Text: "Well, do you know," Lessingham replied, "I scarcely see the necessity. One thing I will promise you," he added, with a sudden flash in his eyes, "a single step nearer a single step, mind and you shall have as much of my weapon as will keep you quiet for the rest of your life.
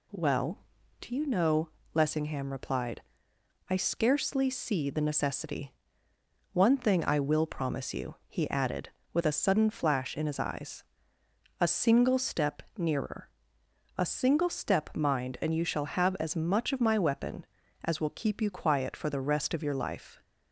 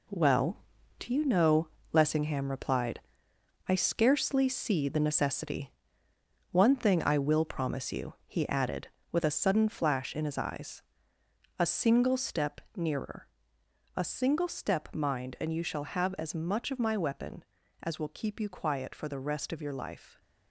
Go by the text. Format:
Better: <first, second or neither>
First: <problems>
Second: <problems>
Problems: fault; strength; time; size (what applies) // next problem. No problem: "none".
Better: first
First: pauses between "nearer" and "a"; noticeable; at 13.2 s; 0.70 s long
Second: gets quieter; strong; throughout; 8.5 dB // pauses between "nearer" and "a"; noticeable; at 13.2 s; 0.70 s long